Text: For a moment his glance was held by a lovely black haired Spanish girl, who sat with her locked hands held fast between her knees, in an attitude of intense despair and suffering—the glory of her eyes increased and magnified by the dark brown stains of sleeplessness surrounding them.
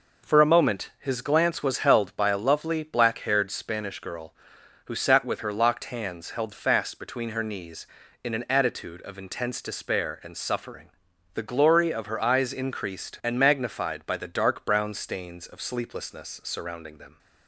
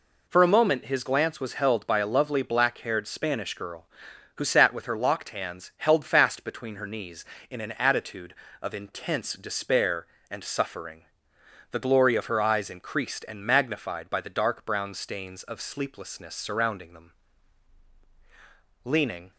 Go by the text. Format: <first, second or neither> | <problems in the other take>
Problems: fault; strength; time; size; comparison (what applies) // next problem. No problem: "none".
first | goes on to say "Leaning"; slight; from 18.8 s on; 0.48 s long